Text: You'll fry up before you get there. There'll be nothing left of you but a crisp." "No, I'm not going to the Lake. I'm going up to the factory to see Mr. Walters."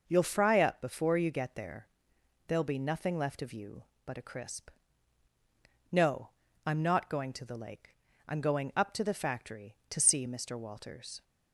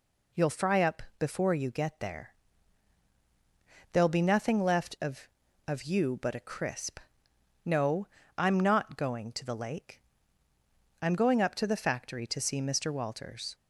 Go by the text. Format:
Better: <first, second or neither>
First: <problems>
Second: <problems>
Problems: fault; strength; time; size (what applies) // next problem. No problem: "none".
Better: first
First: none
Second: pauses between "up" and "before"; slight; at 1.0 s; 0.16 s long // says "of" twice; at 5.6 s